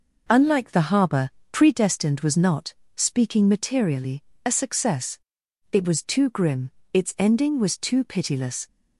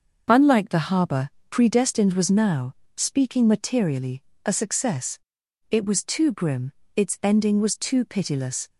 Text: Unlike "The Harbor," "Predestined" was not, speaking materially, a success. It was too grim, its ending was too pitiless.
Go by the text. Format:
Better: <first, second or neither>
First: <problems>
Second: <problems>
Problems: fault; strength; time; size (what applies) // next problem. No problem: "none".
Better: first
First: none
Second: says "now" for "not"; at 2.2 s